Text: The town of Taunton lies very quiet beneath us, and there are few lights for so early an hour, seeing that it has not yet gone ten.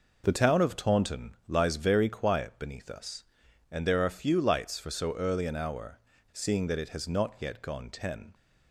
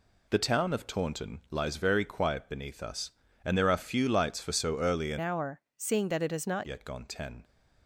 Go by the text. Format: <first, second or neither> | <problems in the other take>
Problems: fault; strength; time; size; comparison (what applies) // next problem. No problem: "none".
first | changes voice from "hour" to "not"; from 5.2 to 6.6 s; 1.4 s long